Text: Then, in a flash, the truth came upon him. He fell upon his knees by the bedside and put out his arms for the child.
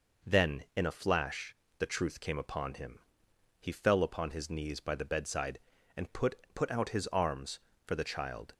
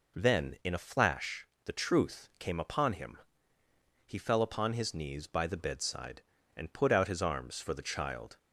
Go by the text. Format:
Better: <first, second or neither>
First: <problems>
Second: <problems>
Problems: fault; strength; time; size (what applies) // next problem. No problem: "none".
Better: second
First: says "put" twice; at 6.5 s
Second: none